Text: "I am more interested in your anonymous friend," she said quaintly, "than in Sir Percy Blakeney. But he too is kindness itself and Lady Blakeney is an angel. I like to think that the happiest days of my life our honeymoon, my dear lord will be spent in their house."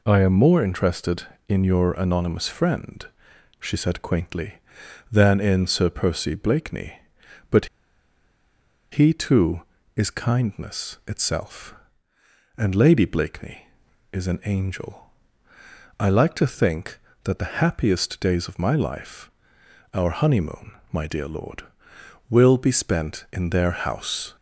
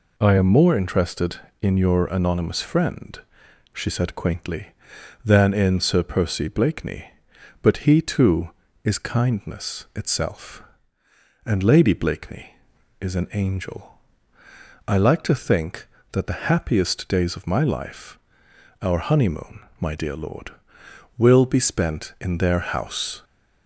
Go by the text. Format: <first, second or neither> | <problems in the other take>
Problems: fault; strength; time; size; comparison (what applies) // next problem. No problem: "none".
second | pauses between "But" and "he"; strong; at 7.6 s; 1.2 s long // pauses between "life" and "our"; noticeable; at 19.2 s; 0.64 s long; noticeable in the second